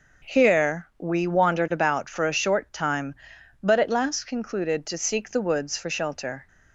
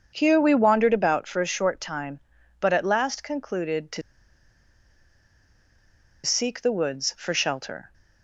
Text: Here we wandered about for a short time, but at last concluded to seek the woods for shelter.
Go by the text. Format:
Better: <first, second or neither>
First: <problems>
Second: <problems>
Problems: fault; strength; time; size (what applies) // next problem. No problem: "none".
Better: first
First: none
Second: starts louder than the rest; until 1.1 s; 7 dB // pauses between "to" and "seek"; strong; at 4.0 s; 2.2 s long